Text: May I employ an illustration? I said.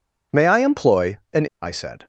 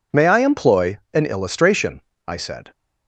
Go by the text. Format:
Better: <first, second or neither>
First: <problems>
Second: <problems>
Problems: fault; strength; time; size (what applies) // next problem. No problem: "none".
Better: second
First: skips "illustration"; at 1.5 s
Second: none